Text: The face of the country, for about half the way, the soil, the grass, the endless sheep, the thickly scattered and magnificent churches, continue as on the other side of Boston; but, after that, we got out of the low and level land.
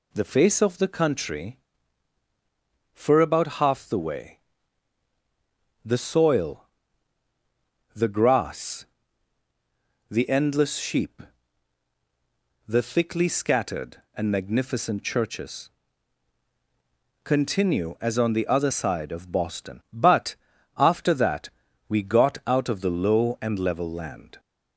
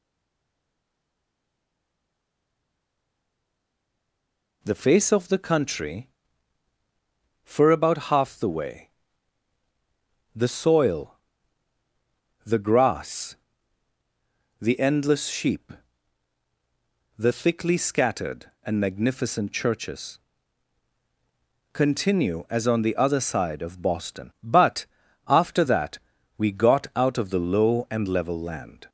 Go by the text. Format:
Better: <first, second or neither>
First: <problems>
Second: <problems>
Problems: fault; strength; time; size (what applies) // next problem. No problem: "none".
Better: first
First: none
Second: stays silent before the first word; strong; until 4.6 s; 4.6 s long